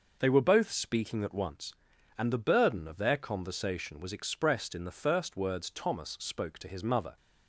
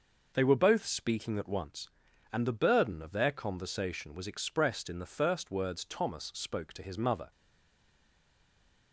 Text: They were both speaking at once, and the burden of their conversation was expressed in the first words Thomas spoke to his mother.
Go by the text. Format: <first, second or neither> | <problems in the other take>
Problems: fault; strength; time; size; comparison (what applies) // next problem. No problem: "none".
first | stays silent after the last word; noticeable; from 7.3 s on; 1.6 s long